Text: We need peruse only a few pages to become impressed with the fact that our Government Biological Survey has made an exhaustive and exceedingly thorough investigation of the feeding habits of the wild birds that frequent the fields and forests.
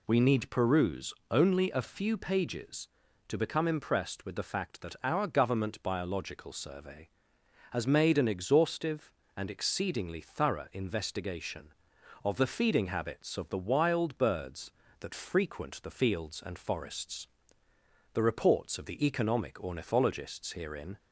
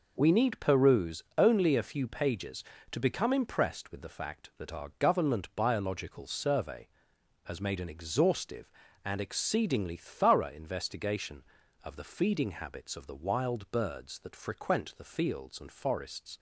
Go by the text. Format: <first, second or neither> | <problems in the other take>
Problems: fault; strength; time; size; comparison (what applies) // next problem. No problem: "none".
second | pauses between "peruse" and "only"; slight; at 1.1 s; 0.16 s long // goes on to say "The reports of the economic ornithologists herein"; strong; from 18.1 s on; 2.8 s long